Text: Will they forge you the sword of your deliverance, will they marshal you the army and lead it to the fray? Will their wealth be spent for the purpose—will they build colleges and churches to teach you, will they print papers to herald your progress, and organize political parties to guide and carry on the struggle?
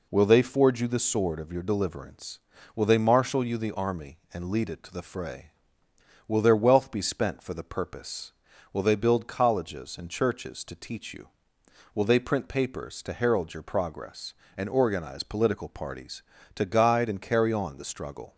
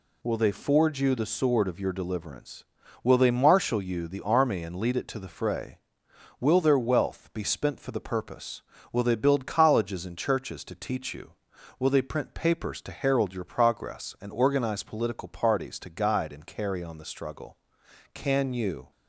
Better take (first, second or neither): first